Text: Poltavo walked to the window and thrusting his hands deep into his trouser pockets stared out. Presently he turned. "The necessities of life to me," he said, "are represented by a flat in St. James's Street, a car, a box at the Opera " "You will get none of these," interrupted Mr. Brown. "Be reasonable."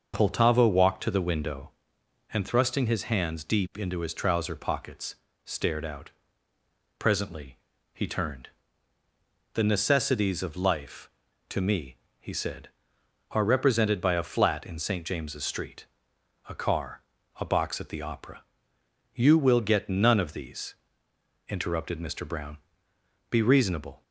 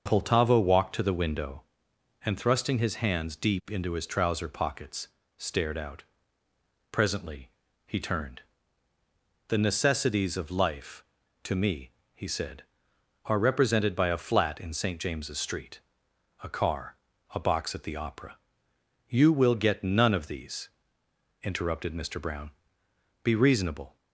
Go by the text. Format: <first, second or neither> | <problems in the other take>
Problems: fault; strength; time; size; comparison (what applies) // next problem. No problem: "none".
neither | starts louder than the rest; noticeable; the same in both // pauses between "pockets" and "stared"; slight; the same in both // pauses between "Presently" and "he"; slight; the same in both